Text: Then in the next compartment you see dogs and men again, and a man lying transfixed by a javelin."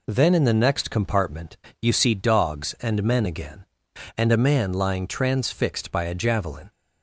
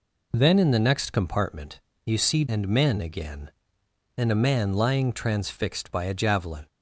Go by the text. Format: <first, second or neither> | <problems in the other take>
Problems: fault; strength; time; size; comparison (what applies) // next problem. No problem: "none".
first | pauses between "compartment" and "you"; slight; at 1.8 s; 0.24 s long; slight in the first // skips "dogs"; at 2.4 s